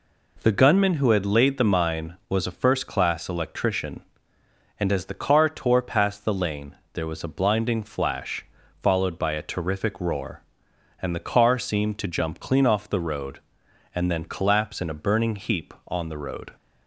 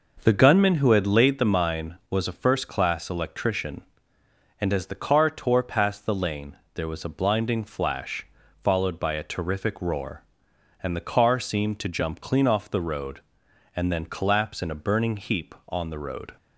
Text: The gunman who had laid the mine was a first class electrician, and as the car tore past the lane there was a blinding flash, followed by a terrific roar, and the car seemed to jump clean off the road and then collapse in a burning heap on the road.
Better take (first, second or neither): first